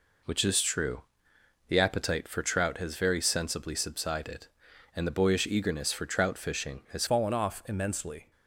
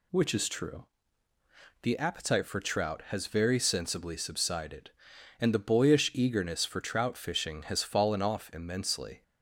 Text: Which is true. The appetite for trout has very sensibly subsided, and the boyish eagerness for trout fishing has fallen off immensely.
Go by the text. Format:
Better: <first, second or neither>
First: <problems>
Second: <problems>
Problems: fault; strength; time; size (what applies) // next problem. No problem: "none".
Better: second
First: changes voice at "fallen"; from 7.0 s on; 1.3 s long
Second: none